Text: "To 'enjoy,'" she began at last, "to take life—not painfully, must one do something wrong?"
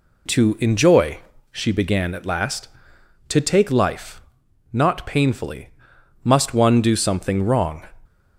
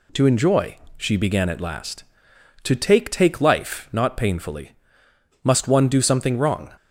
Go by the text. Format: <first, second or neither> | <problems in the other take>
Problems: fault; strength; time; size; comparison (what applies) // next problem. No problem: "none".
first | says "take" twice; at 3.1 s